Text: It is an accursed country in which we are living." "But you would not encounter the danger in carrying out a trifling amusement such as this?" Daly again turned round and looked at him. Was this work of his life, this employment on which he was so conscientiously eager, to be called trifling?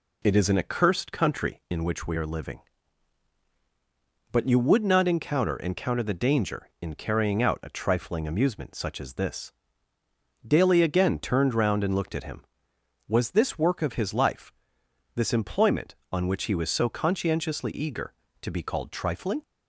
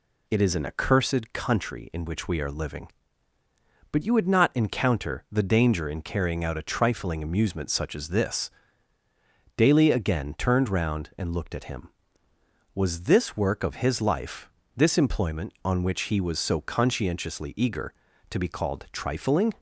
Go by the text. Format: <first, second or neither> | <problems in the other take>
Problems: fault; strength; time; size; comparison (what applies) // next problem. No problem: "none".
second | says "encounter" twice; at 5.5 s